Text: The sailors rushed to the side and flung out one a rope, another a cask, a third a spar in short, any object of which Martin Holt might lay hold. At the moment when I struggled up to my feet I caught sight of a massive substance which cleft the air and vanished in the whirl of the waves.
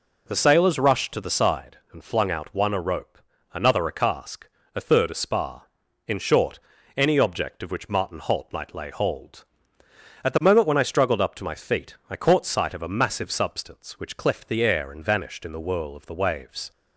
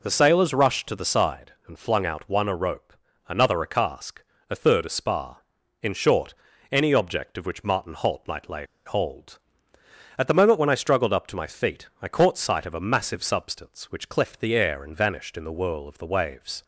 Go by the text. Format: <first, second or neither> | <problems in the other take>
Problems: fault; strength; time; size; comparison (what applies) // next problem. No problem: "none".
first | pauses between "lay" and "hold"; slight; at 8.6 s; 0.19 s long